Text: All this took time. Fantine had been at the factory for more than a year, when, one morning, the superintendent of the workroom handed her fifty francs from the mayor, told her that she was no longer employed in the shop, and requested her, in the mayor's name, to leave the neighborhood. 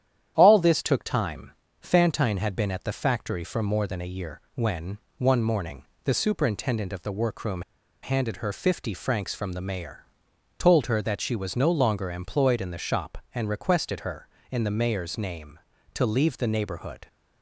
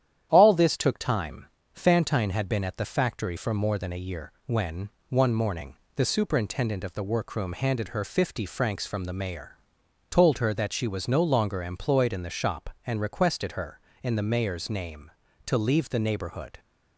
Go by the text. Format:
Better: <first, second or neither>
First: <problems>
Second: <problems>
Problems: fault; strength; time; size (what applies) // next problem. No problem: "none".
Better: second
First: starts louder than the rest; strong; until 1.3 s; 10 dB // pauses between "workroom" and "handed"; at 7.6 s; 0.40 s long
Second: starts louder than the rest; strong; until 1.3 s; 10 dB